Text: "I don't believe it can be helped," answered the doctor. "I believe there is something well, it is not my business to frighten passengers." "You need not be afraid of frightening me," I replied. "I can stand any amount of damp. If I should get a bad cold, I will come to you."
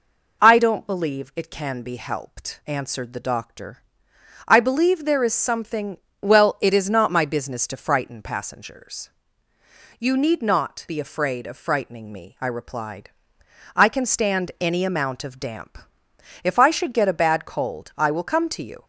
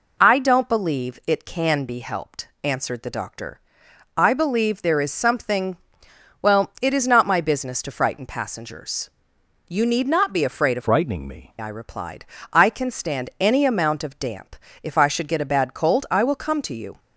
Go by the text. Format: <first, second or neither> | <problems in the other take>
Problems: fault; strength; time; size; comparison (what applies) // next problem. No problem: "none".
first | pauses between "something" and "well"; noticeable; at 5.7 s; 0.64 s long; slight in the first // changes voice from "frightening" to "me"; from 10.7 to 11.5 s; 0.8 s long